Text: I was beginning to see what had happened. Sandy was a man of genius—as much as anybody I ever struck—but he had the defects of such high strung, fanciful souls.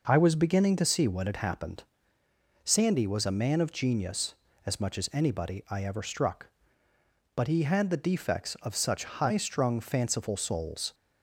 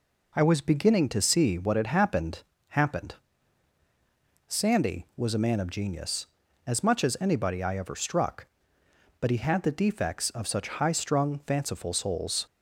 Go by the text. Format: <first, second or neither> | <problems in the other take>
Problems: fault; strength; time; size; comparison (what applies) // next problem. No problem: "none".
first | says "happened" twice; at 2.6 s